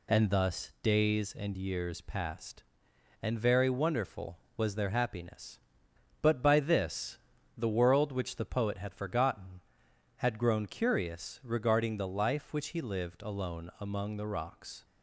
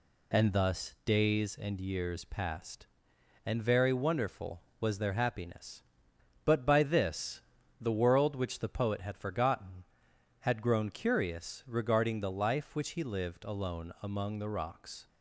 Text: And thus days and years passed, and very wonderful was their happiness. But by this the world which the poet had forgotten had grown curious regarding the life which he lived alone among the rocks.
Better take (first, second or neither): neither